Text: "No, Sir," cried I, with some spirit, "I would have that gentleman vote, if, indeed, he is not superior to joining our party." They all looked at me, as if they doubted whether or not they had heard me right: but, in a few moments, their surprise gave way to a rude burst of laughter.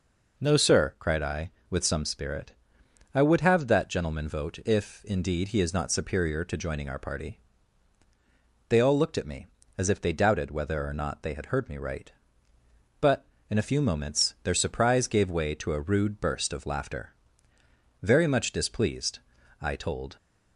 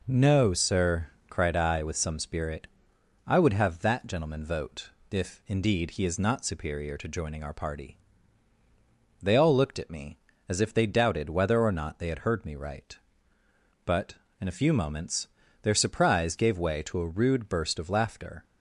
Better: second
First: goes on to say "Very much displeased I told"; strong; from 18.0 s on; 2.1 s long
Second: none

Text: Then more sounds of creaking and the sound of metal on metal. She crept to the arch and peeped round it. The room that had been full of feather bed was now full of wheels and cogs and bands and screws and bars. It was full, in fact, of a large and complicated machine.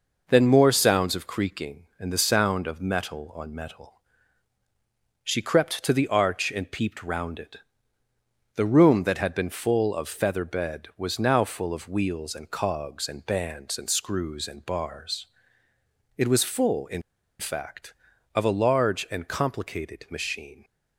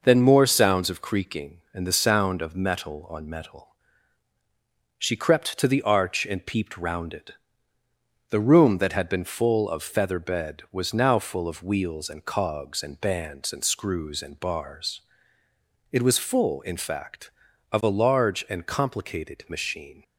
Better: second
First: pauses between "in" and "fact"; at 17.0 s; 0.38 s long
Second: none

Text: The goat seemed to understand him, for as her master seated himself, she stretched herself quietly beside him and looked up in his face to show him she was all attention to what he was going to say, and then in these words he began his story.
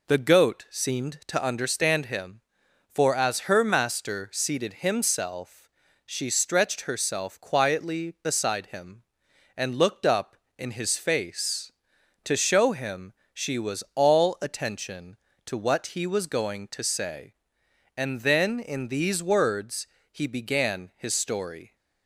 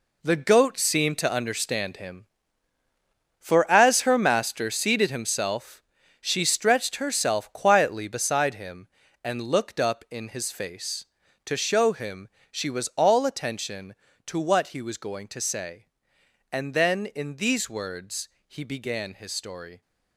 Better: first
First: pauses between "him" and "she"; slight; at 13.1 s; 0.20 s long // pauses between "words" and "he"; slight; at 19.8 s; 0.24 s long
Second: gets quieter; strong; throughout; 10 dB // pauses between "him" and "she"; slight; at 12.2 s; 0.22 s long // pauses between "words" and "he"; slight; at 18.2 s; 0.18 s long

